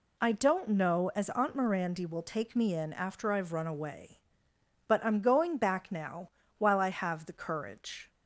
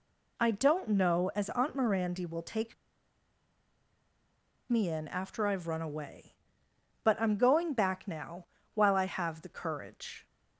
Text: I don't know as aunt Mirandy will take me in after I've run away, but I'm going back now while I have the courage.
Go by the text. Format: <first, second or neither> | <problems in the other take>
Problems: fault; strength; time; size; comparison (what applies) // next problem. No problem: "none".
first | pauses between "take" and "me"; strong; at 2.7 s; 1.9 s long // pauses between "now" and "while"; slight; at 8.4 s; 0.30 s long; slight in the first